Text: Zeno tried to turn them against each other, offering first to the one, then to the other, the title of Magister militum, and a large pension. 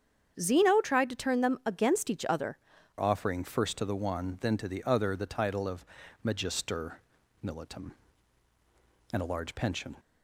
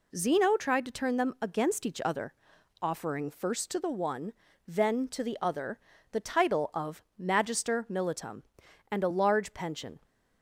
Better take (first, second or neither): second